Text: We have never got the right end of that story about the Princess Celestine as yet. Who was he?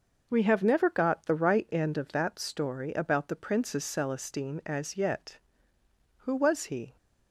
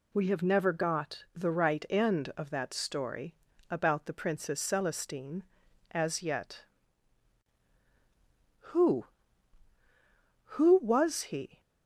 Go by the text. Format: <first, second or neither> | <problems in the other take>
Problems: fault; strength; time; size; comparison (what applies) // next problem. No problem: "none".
first | pauses between "story" and "about"; slight; at 3.3 s; 0.36 s long // says "Who" twice; at 10.4 s